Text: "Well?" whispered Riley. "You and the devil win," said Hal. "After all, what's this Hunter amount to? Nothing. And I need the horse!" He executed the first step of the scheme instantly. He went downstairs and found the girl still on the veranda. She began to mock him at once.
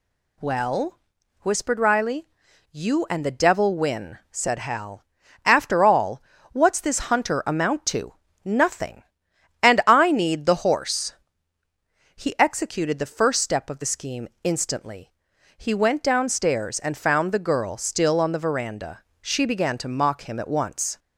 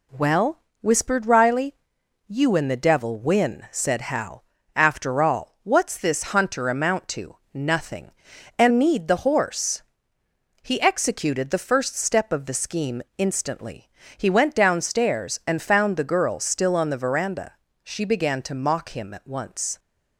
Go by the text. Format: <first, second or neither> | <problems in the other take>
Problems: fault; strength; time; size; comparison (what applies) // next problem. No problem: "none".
first | skips "I"; at 8.6 s // pauses between "scheme" and "instantly"; slight; at 13.0 s; 0.16 s long